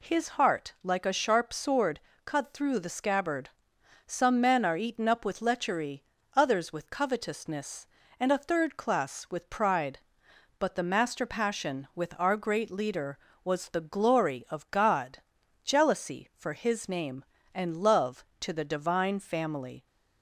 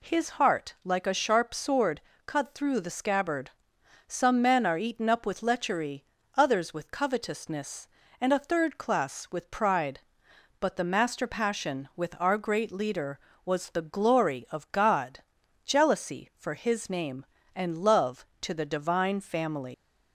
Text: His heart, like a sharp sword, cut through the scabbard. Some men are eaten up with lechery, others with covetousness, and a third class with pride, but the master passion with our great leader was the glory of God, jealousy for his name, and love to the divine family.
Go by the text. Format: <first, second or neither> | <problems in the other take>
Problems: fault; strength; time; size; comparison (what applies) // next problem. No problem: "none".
first | leaves "family" unfinished; at 19.7 s; 120 ms